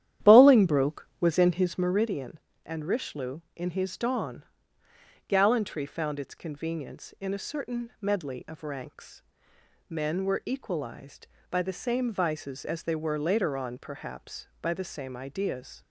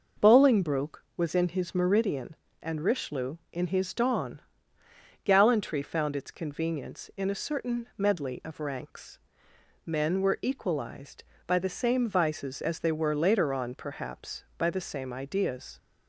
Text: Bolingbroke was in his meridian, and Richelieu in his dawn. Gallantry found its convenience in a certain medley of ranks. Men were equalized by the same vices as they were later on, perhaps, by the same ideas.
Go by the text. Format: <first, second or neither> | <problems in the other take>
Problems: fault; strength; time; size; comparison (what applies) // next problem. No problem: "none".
second | starts louder than the rest; strong; until 1.9 s; 11 dB